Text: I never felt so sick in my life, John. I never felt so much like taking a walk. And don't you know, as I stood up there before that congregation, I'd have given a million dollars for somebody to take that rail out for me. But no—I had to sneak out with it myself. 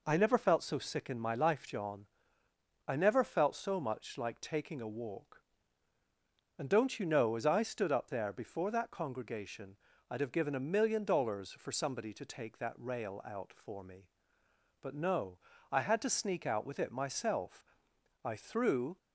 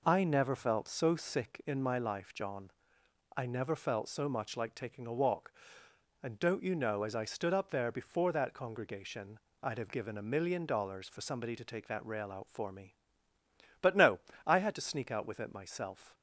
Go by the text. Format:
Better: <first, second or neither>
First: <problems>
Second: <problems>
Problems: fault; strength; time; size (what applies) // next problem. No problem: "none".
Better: second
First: goes on to say "I threw"; noticeable; from 18.2 s on; 0.72 s long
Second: none